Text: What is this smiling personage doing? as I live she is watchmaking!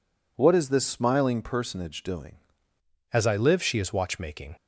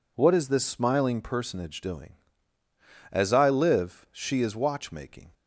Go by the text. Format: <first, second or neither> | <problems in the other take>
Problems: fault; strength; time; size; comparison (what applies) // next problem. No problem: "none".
second | changes voice at "as"; from 3.1 s on; 1.4 s long